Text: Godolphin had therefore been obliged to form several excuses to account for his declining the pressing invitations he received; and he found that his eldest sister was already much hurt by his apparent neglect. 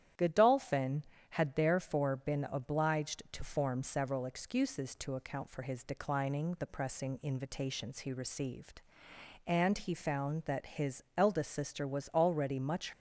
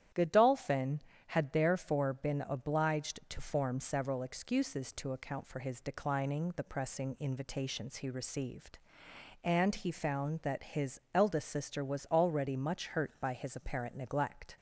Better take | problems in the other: second | starts louder than the rest; strong; until 1.4 s; 11 dB; strong in the second // pauses between "his" and "eldest"; slight; at 11.0 s; 0.16 s long; slight in the second // stops before "hurt by his apparent neglect"; at 12.9 s

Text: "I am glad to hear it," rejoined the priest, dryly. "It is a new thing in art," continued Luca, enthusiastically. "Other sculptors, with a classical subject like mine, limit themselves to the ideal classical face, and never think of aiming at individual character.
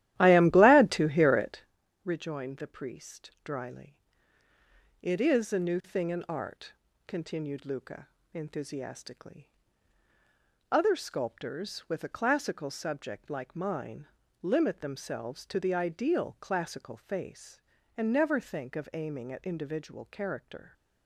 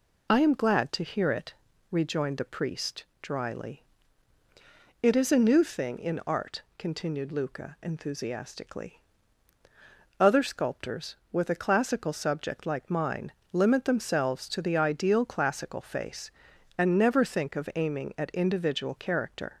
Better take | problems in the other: second | starts louder than the rest; strong; until 1.7 s; 13.5 dB

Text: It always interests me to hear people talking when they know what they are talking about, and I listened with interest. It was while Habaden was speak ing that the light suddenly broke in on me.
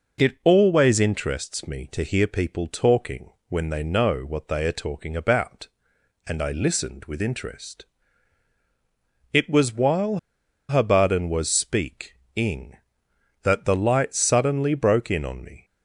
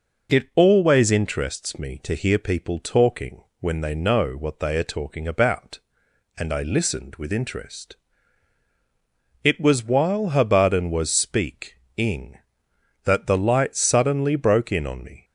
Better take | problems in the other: second | pauses between "talking" and "when"; slight; at 3.2 s; 0.18 s long; slight in the second // pauses between "while" and "Habaden"; noticeable; at 10.1 s; 0.49 s long // pauses between "speak" and "ing"; slight; at 12.1 s; 0.22 s long; slight in the second

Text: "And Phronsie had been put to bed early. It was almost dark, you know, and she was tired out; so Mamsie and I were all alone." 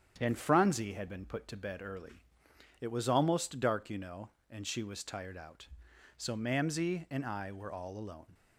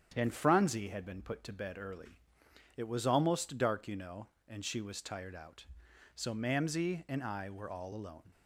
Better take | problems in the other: neither | starts louder than the rest; strong; the same in both

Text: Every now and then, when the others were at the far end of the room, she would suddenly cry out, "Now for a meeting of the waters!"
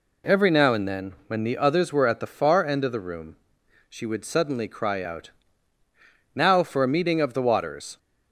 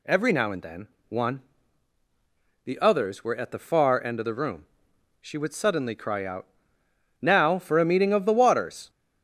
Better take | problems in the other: first | says "one" for "when"; at 1.0 s

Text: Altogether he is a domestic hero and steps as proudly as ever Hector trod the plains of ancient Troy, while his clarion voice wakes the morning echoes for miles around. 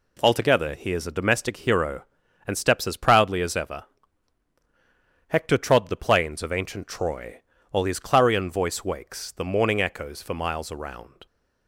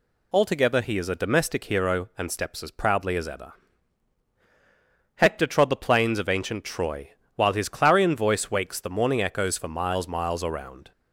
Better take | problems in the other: first | pauses between "ever" and "Hector"; strong; at 3.5 s; 1.6 s long; strong in the first // says "miles" twice; at 10.0 s

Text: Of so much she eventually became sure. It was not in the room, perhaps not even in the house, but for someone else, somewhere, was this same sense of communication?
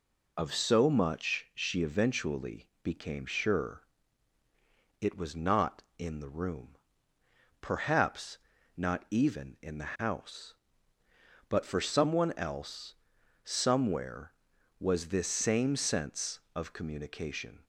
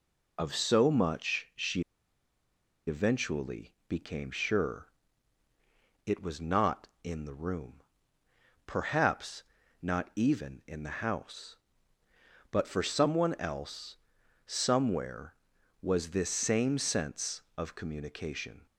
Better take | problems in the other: first | pauses between "she" and "eventually"; at 1.8 s; 1.0 s long // pauses between "eventually" and "became"; slight; at 3.7 s; 0.16 s long; slight in the first // pauses between "perhaps" and "not"; at 9.4 s; 0.38 s long; also in the first

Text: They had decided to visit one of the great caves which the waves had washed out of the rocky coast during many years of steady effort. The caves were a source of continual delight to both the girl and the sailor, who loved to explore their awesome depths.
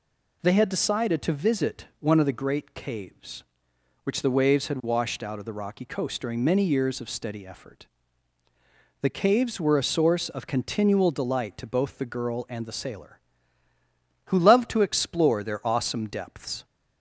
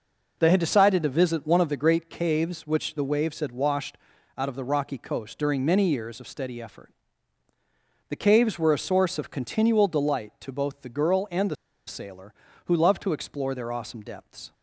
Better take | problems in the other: first | pauses between "washed" and "out"; at 3.9 s; 0.40 s long // pauses between "the" and "sailor"; slight; at 11.5 s; 0.33 s long

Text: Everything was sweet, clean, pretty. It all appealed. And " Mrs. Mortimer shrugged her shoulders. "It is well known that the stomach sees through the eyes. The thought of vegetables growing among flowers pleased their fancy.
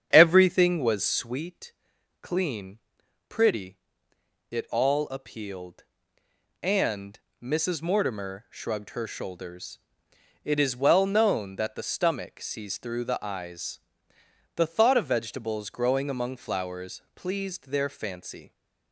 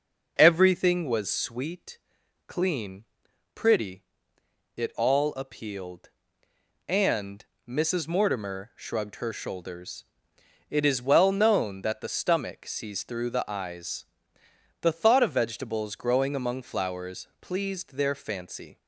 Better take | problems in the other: second | starts louder than the rest; strong; until 1.4 s; 8 dB // pauses between "flowers" and "pleased"; slight; at 16.9 s; 0.16 s long; slight in the second

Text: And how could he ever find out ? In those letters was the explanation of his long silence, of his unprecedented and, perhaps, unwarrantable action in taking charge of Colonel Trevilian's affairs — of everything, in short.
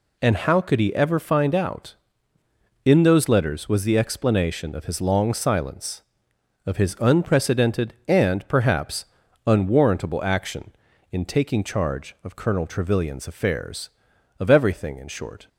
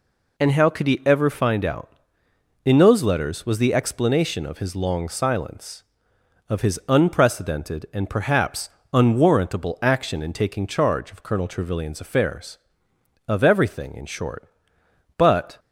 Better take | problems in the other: first | goes on to say "But"; slight; from 15.1 s on; 0.42 s long

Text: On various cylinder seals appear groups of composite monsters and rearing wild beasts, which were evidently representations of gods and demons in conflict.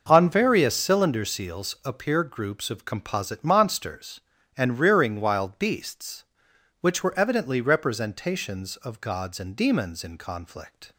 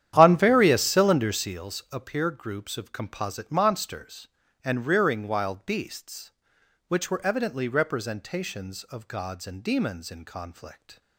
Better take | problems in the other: first | starts louder than the rest; strong; until 1.6 s; 10.5 dB

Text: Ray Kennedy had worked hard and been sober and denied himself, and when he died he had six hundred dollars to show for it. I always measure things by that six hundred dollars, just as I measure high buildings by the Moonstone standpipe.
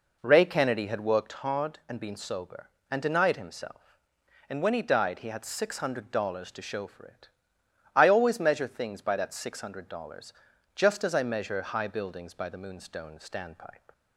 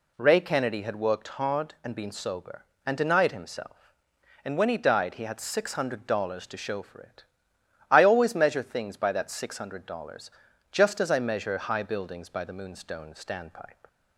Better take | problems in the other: second | starts louder than the rest; noticeable; until 1.4 s; 4.5 dB

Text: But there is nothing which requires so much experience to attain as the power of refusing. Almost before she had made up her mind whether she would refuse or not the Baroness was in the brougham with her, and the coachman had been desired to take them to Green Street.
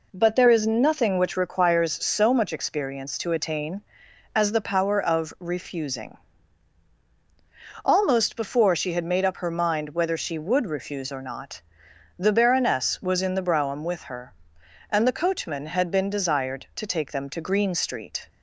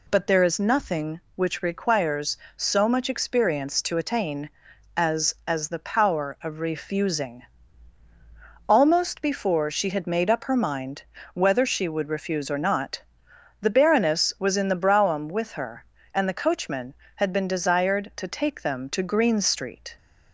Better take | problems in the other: first | says "as" twice; at 5.4 s // pauses between "mind" and "whether"; slight; at 11.0 s; 0.32 s long // pauses between "not" and "the"; noticeable; at 13.0 s; 0.58 s long; noticeable in the first

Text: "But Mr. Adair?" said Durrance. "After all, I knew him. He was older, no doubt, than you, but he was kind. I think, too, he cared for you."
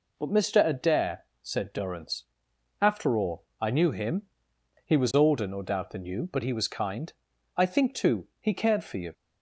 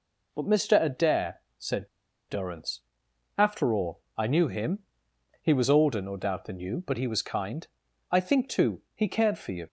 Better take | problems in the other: first | pauses between "said" and "Durrance"; at 1.8 s; 0.40 s long

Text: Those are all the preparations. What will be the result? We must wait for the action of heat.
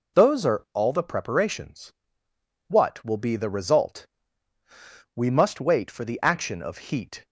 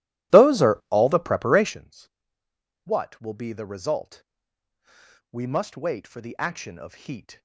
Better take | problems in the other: first | starts louder than the rest; strong; until 1.8 s; 14.5 dB

